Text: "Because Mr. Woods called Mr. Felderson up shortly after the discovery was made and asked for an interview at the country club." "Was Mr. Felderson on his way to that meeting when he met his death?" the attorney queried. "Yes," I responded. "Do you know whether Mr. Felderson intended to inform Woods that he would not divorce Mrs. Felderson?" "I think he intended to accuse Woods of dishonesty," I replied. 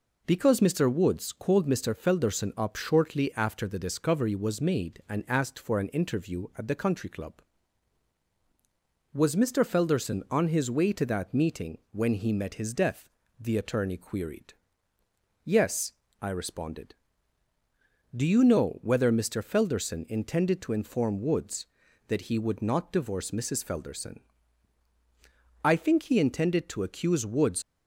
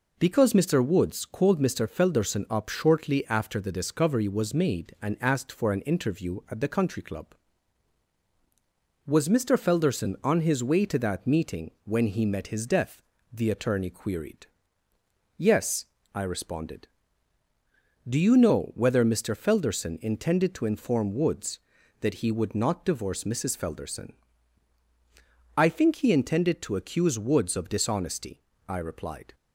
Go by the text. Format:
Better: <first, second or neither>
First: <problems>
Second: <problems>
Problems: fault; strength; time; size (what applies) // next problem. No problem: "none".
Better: second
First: stops before "of dishonesty I replied"; at 27.6 s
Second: none